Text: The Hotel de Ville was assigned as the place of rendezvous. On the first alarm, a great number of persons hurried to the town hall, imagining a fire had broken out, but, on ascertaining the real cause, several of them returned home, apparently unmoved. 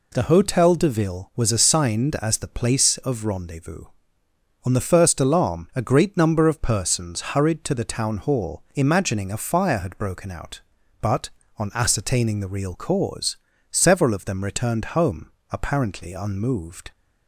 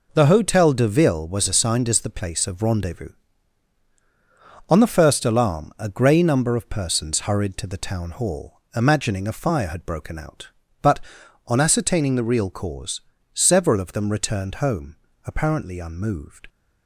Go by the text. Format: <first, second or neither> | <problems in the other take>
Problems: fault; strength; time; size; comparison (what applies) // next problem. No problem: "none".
first | says "grey" for "great"; at 5.8 s